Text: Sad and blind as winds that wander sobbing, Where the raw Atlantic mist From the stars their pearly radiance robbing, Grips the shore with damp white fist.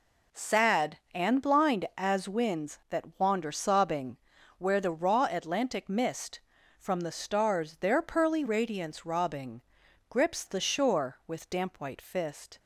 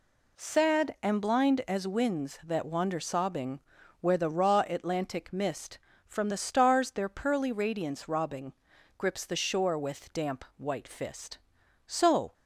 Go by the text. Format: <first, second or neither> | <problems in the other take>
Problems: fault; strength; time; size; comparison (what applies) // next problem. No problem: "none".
first | goes on to say "So"; slight; from 11.8 s on; 0.48 s long